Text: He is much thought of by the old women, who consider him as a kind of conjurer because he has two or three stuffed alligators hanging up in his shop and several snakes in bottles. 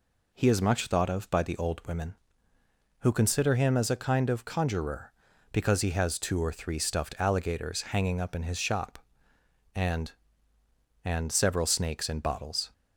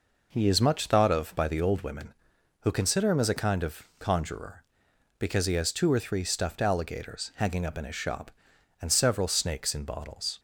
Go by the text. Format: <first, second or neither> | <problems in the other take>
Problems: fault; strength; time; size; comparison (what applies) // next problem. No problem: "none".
second | says "and" twice; at 11.0 s